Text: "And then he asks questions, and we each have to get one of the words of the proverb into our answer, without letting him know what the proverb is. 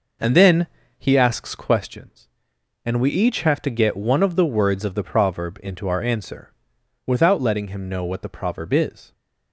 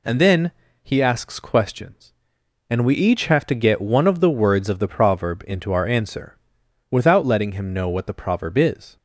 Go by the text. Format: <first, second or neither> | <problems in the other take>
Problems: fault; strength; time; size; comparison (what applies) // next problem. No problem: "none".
second | starts louder than the rest; noticeable; until 1.8 s; 5 dB // pauses between "then" and "he"; slight; at 0.6 s; 0.32 s long; slight in the second